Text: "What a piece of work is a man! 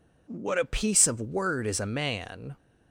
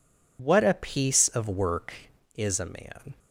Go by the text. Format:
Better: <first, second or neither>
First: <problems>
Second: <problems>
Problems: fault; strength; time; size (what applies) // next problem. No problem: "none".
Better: second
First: says "word" for "work"; at 1.2 s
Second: none